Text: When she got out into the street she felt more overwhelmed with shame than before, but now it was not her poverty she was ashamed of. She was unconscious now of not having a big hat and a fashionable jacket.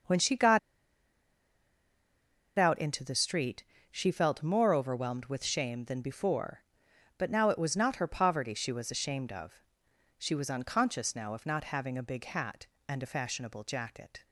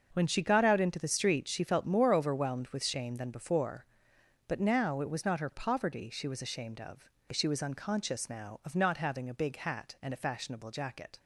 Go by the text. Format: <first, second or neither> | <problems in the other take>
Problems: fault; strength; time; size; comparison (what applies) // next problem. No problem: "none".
second | starts louder than the rest; until 3.0 s; 6.5 dB; also in the second // pauses between "got" and "out"; strong; at 0.5 s; 1.9 s long // pauses between "street" and "she"; slight; at 3.6 s; 0.28 s long